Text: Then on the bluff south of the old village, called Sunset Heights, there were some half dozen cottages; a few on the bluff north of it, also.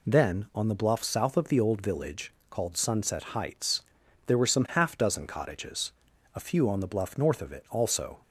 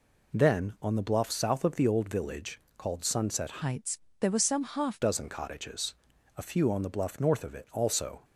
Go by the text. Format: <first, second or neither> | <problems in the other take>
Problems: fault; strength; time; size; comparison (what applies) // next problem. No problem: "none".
first | changes voice from "Heights" to "half"; from 3.6 to 5.0 s; 1.4 s long